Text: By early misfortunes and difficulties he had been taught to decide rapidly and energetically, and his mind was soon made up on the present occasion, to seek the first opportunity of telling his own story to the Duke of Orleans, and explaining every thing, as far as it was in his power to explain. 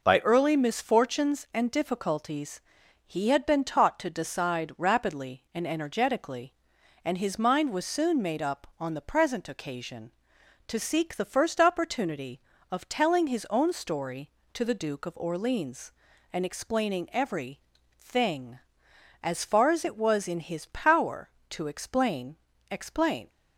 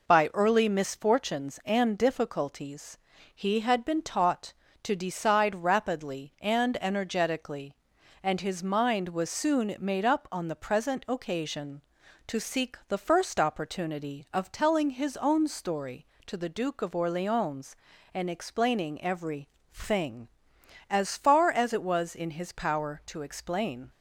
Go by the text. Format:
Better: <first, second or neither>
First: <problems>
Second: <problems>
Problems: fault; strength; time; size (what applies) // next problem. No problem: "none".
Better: second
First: pauses between "difficulties" and "he"; noticeable; at 2.5 s; 0.48 s long // pauses between "every" and "thing"; at 17.5 s; 0.42 s long // says "explain" twice; at 22.6 s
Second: pauses between "difficulties" and "he"; at 2.9 s; 0.38 s long // pauses between "every" and "thing"; slight; at 19.4 s; 0.24 s long